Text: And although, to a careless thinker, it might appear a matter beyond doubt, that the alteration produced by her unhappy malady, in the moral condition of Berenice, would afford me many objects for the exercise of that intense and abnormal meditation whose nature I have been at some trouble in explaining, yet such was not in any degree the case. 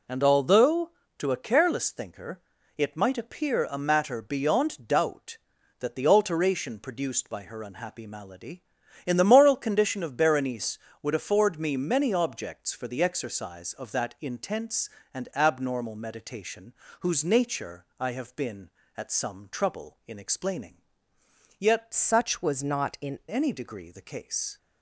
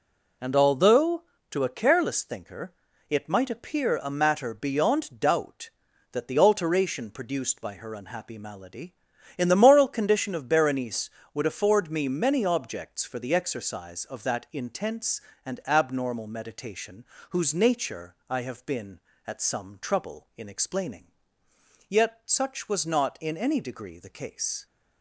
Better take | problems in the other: second | pauses between "meditation" and "whose"; slight; at 16.7 s; 0.28 s long; slight in the second // pauses between "nature" and "I"; slight; at 17.8 s; 0.16 s long; slight in the second // changes voice from "such" to "in"; from 21.9 to 23.1 s; 1.2 s long

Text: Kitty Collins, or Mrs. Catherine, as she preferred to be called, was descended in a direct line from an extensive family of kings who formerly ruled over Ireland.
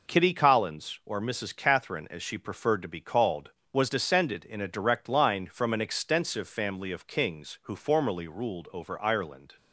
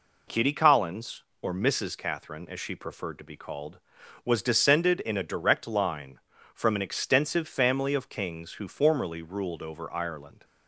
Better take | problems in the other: neither | none

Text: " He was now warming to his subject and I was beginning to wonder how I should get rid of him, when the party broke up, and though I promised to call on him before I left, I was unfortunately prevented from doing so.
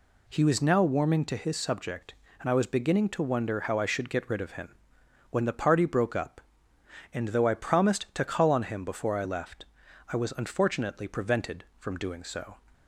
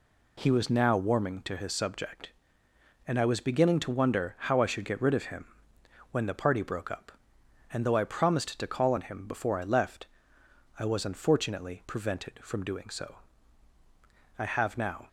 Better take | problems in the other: first | goes on to say "I have now"; noticeable; from 14.3 s on; 0.70 s long

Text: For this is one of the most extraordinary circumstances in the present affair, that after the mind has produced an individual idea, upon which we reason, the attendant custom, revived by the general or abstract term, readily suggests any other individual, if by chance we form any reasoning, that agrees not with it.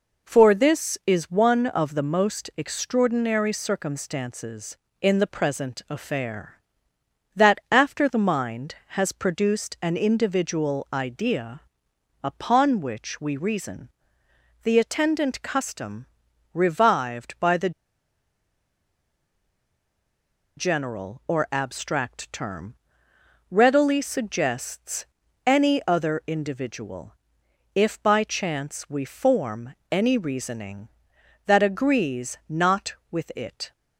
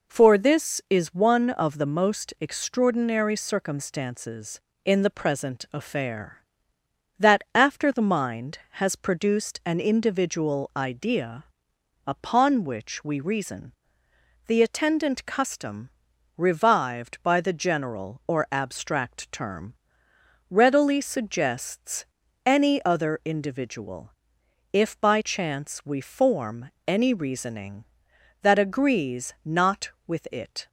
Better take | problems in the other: second | pauses between "the" and "general"; strong; at 17.7 s; 2.8 s long // pauses between "suggests" and "any"; at 25.0 s; 0.40 s long; also in the second // pauses between "form" and "any"; slight; at 29.7 s; 0.16 s long; slight in the second

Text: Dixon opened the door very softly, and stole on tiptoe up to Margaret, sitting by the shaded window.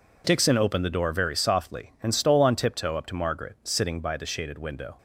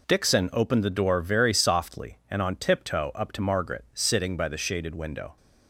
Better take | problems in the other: first | skips "stole"; at 2.4 s

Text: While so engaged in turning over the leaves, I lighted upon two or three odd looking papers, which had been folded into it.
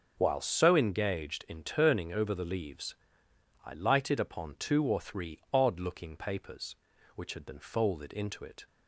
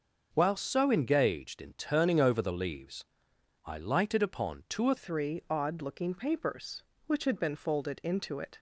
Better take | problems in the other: first | starts louder than the rest; until 1.3 s; 6.5 dB // changes voice at "three"; from 4.9 s on; 3.6 s long

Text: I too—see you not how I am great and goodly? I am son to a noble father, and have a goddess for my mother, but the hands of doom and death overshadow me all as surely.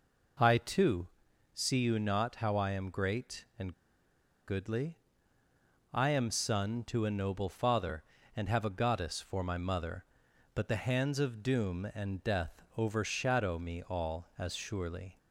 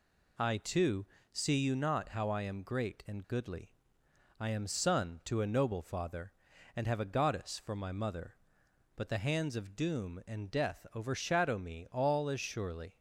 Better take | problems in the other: second | pauses between "and" and "goodly"; noticeable; at 3.7 s; 0.75 s long // pauses between "death" and "overshadow"; slight; at 12.6 s; 0.16 s long

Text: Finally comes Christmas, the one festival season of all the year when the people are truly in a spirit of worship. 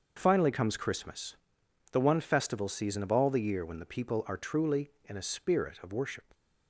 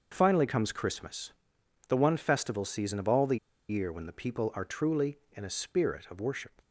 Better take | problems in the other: first | starts louder than the rest; noticeable; until 1.1 s; 6 dB; noticeable in the first // pauses between "the" and "year"; slight; at 3.3 s; 0.30 s long

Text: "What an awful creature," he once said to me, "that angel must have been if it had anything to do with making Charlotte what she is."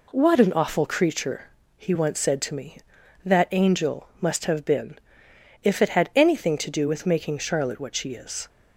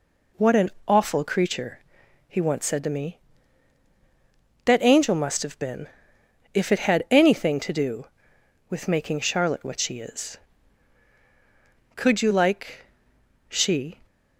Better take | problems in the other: first | pauses between "an" and "awful"; slight; at 0.7 s; 0.16 s long // pauses between "been" and "if"; noticeable; at 5.8 s; 0.69 s long; noticeable in the first // goes on to say "Could you like she"; strong; from 11.9 s on; 2.0 s long

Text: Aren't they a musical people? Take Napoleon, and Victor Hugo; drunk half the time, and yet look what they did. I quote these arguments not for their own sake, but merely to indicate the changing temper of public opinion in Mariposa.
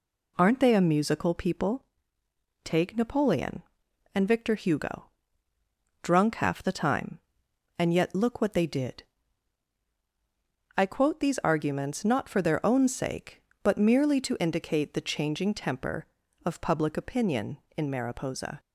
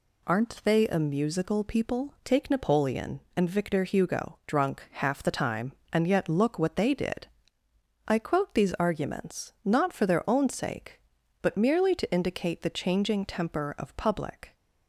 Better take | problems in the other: first | stops before "opinion in Mariposa"; at 14.5 s

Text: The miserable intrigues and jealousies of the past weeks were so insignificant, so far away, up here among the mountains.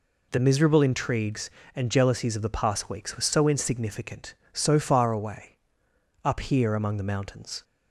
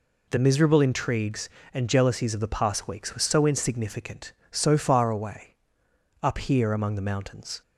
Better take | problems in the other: neither | none

